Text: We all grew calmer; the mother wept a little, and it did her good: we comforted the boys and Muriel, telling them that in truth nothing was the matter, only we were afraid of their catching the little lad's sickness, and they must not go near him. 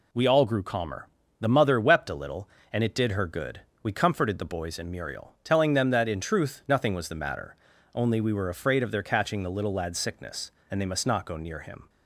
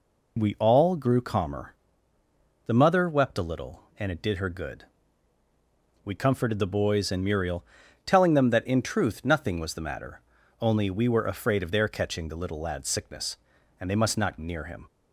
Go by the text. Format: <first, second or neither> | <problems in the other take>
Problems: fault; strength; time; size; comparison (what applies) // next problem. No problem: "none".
first | skips "go"; at 14.3 s